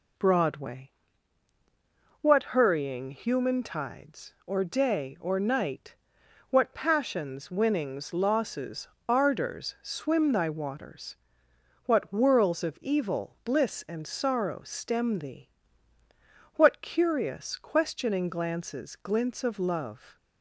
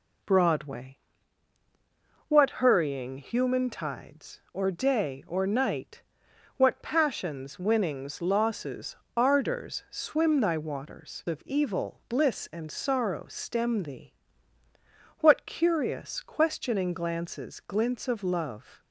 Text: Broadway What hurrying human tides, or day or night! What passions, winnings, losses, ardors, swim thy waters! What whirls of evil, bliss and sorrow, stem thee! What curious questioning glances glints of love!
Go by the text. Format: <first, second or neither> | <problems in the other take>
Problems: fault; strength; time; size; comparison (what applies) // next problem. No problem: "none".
first | pauses between "Broadway" and "What"; strong; at 0.9 s; 1.3 s long; strong in the first // skips "What whirls"; at 11.2 s